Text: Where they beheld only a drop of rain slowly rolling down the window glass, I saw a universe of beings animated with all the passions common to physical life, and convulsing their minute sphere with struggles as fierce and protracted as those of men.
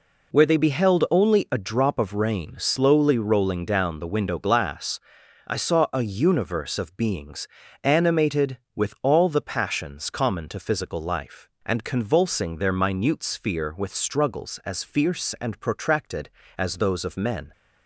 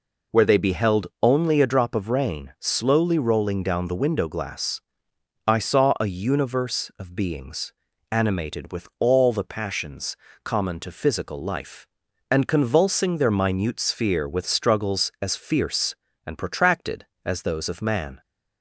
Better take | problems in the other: first | pauses between "beings" and "animated"; at 7.7 s; 0.40 s long; slight in the first // pauses between "passions" and "common"; slight; at 10.1 s; 0.30 s long // says "man" for "men"; at 17.8 s

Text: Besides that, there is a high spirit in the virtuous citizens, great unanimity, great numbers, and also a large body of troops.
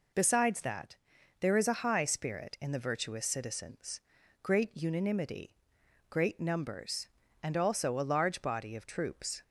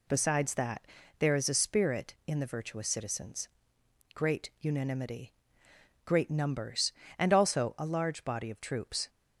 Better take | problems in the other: first | skips "high"; at 1.5 s

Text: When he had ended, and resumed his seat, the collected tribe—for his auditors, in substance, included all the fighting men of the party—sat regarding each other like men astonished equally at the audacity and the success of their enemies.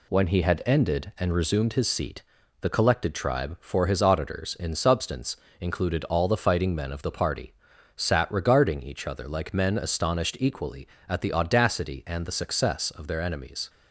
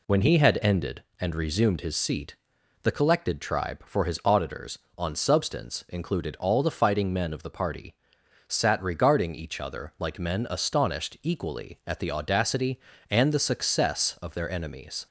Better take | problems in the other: first | says "on" for "in"; at 4.9 s

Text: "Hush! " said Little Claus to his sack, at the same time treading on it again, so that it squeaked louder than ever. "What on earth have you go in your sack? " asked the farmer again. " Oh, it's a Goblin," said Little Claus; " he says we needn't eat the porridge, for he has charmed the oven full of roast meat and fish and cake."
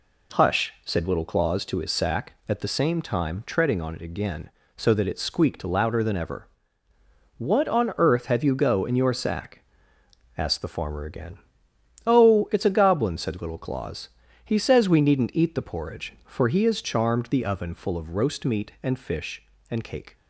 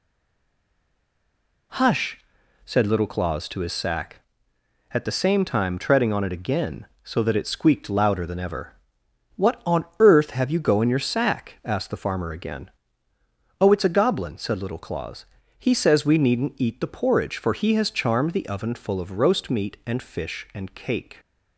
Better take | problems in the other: first | stays silent before the first word; noticeable; until 1.7 s; 1.7 s long // pauses between "on" and "earth"; slight; at 9.8 s; 0.16 s long

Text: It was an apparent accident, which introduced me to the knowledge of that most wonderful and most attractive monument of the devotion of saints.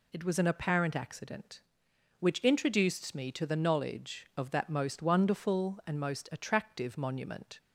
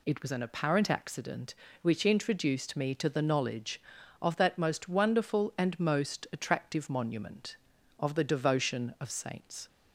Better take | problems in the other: second | stops before "of the devotion of saints"; at 7.5 s

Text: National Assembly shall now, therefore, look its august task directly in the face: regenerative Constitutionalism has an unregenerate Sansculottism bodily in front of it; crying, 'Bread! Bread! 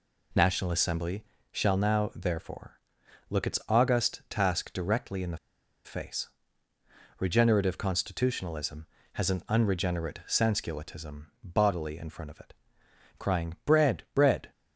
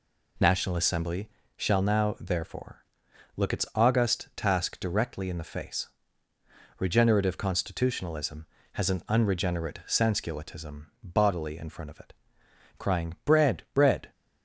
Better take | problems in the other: second | pauses between "Assembly" and "shall"; slight; at 1.2 s; 0.26 s long; slight in the second // pauses between "the" and "face"; noticeable; at 5.3 s; 0.48 s long // pauses between "Sansculottism" and "bodily"; slight; at 11.2 s; 0.18 s long; slight in the second

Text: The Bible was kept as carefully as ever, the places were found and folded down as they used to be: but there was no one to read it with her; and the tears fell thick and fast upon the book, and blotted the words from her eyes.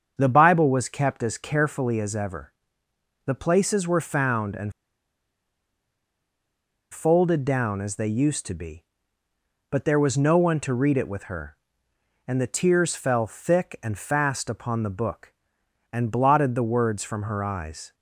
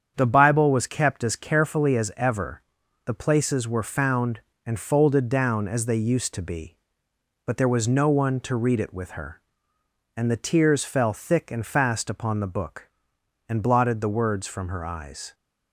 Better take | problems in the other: second | starts louder than the rest; until 1.1 s; 7 dB; strong in the second // pauses between "and" and "folded"; strong; at 4.7 s; 2.1 s long

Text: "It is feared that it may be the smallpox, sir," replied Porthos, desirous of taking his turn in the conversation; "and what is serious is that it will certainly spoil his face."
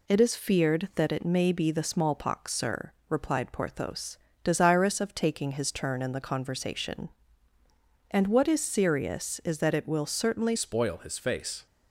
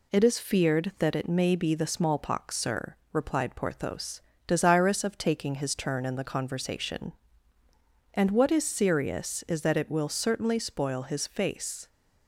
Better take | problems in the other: second | changes voice at "spoil"; from 10.5 s on; 1.1 s long

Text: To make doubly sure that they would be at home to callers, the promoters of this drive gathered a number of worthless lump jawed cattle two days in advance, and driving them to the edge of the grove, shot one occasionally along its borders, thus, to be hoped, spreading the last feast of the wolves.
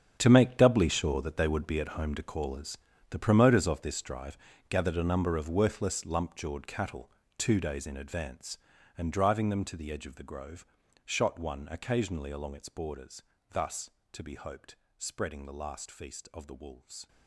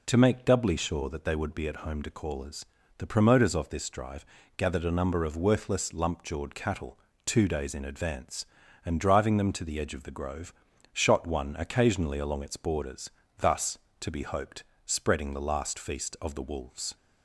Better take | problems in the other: second | gets quieter; strong; throughout; 14.5 dB // pauses between "drive" and "gathered"; slight; at 4.3 s; 0.32 s long; slight in the second // pauses between "cattle" and "two"; slight; at 7.1 s; 0.24 s long; slight in the second

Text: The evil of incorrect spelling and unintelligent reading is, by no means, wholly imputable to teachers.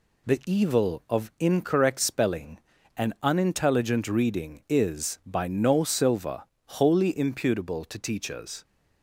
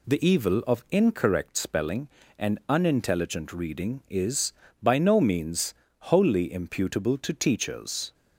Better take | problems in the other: second | says "silver" for "means"; at 5.8 s

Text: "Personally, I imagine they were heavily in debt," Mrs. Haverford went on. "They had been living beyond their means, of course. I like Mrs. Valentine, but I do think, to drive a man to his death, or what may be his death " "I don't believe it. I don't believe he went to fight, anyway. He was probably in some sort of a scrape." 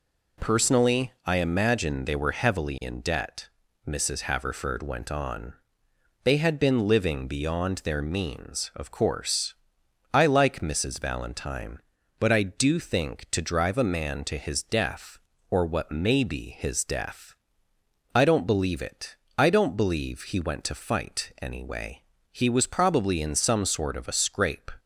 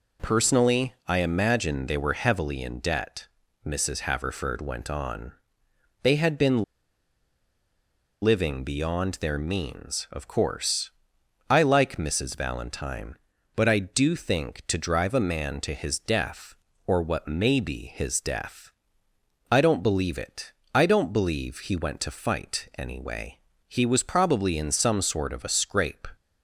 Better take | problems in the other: first | pauses between "been" and "living"; strong; at 6.6 s; 1.5 s long

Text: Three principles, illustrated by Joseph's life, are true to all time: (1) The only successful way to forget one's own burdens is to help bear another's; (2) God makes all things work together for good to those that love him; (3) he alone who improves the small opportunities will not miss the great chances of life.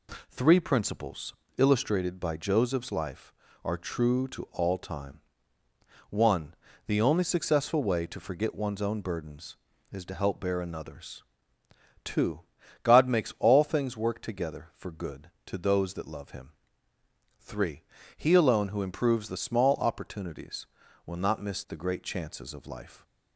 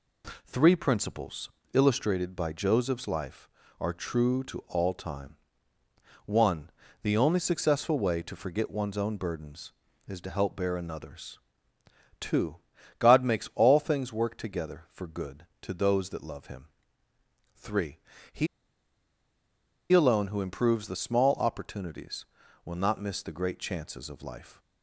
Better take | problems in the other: first | pauses between "he" and "alone"; strong; at 18.4 s; 1.4 s long

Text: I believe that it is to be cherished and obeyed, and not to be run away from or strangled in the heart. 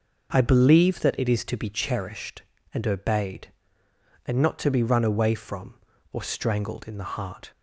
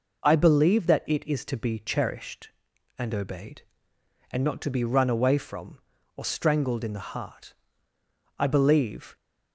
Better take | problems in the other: first | goes on to say "I believe"; noticeable; from 8.3 s on; 0.76 s long

